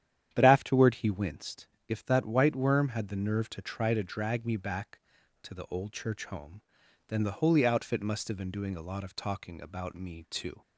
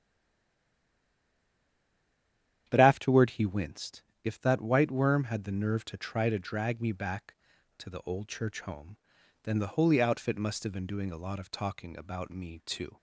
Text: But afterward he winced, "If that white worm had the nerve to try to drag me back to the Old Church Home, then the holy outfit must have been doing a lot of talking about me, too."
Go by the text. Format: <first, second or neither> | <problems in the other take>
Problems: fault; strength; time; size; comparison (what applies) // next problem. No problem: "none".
first | stays silent before the first word; strong; until 2.6 s; 2.6 s long // starts louder than the rest; strong; until 3.6 s; 10 dB; strong in the first